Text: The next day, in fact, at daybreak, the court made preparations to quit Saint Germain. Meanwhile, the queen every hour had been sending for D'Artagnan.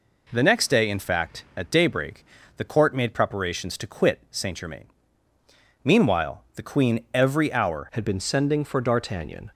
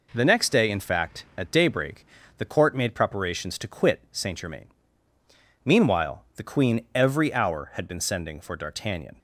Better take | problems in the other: second | changes voice at "had"; from 7.9 s on; 1.6 s long

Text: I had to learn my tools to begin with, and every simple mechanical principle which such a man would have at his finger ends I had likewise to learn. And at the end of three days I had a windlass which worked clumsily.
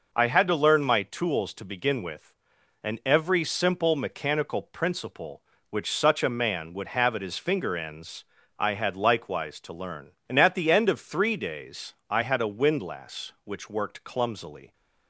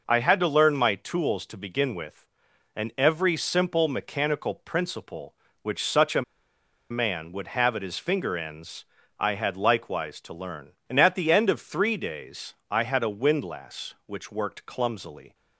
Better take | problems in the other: first | pauses between "a" and "man"; noticeable; at 6.2 s; 0.68 s long // pauses between "ends" and "I"; slight; at 8.8 s; 0.34 s long; slight in the first // pauses between "days" and "I"; slight; at 12.5 s; 0.16 s long; slight in the first

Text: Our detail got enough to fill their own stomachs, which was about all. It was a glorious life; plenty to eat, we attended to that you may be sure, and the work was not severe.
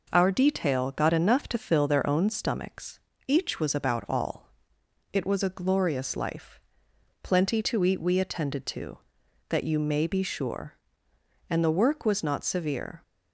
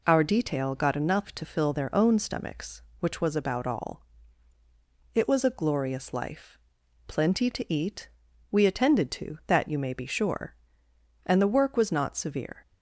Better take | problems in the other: second | says "each" for "which"; at 3.2 s

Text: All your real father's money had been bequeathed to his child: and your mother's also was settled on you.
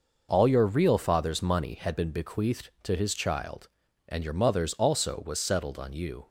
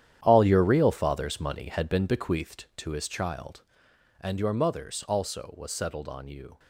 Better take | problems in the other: first | gets quieter; strong; throughout; 13 dB

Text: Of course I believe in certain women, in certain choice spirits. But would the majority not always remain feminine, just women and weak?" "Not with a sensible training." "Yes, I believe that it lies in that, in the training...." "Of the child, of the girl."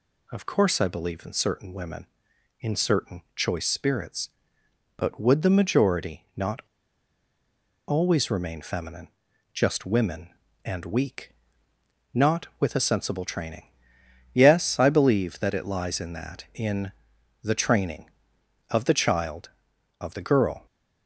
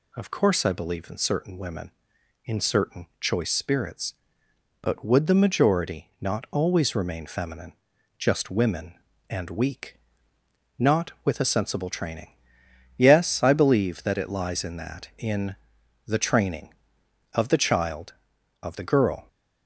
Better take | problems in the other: second | pauses between "not" and "always"; strong; at 6.5 s; 1.2 s long // pauses between "in" and "the"; noticeable; at 16.9 s; 0.50 s long; noticeable in the second

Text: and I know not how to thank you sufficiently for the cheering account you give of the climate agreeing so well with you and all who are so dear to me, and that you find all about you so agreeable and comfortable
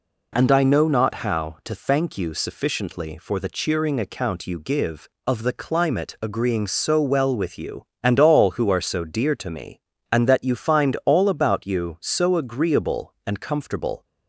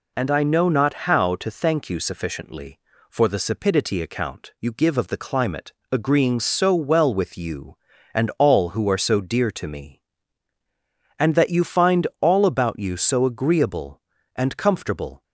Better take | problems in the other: first | says "sapidity" for "cheering"; at 3.3 s // pauses between "climate" and "agreeing"; slight; at 5.7 s; 0.20 s long

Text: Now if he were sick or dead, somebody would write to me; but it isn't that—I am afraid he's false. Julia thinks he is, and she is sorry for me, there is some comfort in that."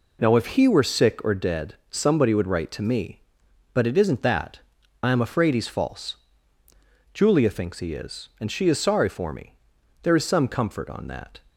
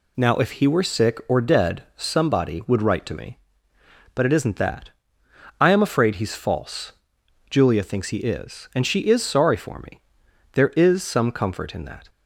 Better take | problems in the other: second | says "on" for "in"; at 10.8 s

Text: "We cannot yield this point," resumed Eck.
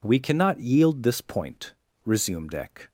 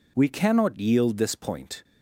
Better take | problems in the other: first | stops before "resumed Eck"; at 1.8 s

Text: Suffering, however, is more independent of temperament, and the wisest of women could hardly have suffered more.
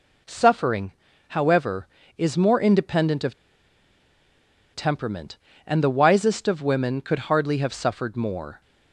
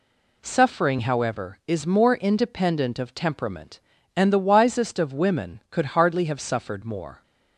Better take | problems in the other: second | pauses between "of" and "temperament"; strong; at 3.3 s; 1.3 s long

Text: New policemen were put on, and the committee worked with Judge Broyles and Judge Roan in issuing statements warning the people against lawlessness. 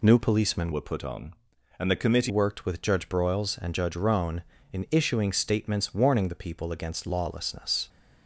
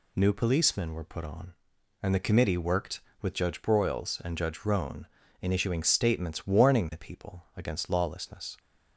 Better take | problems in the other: second | changes voice from "were" to "committee"; from 0.7 to 2.3 s; 1.6 s long

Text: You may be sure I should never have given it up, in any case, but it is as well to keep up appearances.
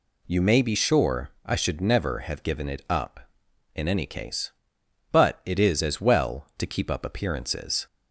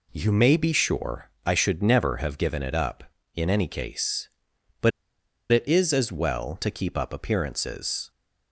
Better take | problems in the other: first | pauses between "sure" and "I"; slight; at 1.2 s; 0.16 s long; slight in the first // pauses between "but" and "it"; noticeable; at 4.9 s; 0.61 s long

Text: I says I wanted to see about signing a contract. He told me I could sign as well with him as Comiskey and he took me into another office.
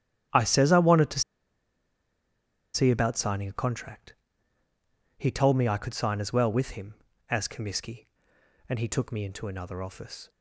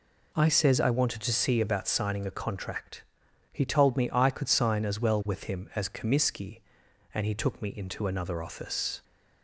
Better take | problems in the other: second | starts louder than the rest; strong; until 2.8 s; 10 dB // pauses between "to" and "see"; strong; at 1.2 s; 1.5 s long

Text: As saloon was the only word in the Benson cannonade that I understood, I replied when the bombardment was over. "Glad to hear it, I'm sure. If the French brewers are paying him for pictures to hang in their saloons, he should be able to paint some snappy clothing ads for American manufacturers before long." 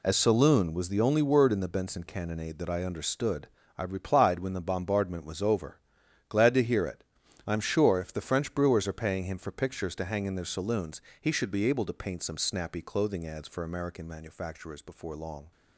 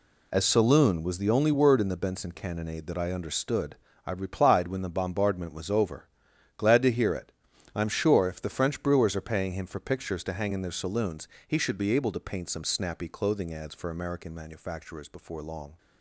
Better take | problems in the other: neither | none

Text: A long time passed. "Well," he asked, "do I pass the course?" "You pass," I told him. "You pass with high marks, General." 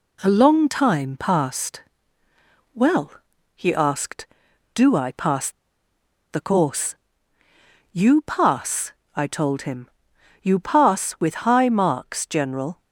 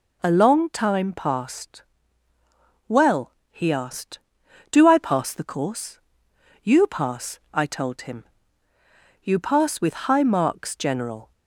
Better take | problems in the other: second | pauses between "pass" and "the"; noticeable; at 5.4 s; 0.81 s long

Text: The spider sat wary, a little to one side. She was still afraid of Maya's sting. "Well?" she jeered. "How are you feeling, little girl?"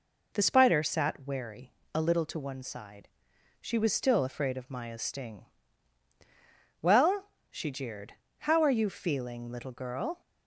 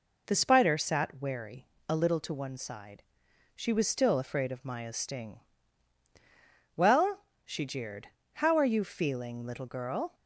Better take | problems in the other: neither | none

